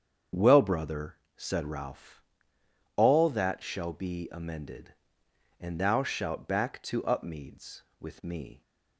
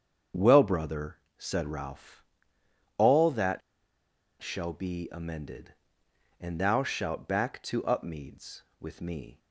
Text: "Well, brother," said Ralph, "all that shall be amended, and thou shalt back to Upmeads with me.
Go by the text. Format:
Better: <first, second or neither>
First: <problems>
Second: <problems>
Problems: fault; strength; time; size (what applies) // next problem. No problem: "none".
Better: first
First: starts louder than the rest; strong; until 1.5 s; 7.5 dB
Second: starts louder than the rest; strong; until 1.5 s; 7.5 dB // pauses between "that" and "shall"; noticeable; at 3.6 s; 0.81 s long